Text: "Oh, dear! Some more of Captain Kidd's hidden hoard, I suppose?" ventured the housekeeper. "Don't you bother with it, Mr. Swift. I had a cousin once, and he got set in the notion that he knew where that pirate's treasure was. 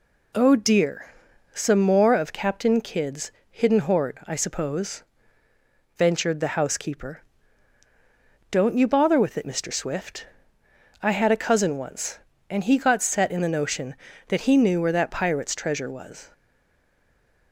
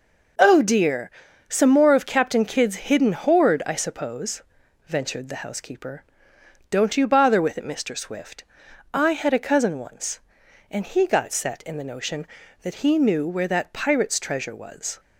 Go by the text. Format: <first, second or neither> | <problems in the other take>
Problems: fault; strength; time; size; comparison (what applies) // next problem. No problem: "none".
second | pauses between "Kidd's" and "hidden"; slight; at 3.3 s; 0.20 s long // stays silent after the last word; noticeable; from 16.3 s on; 1.2 s long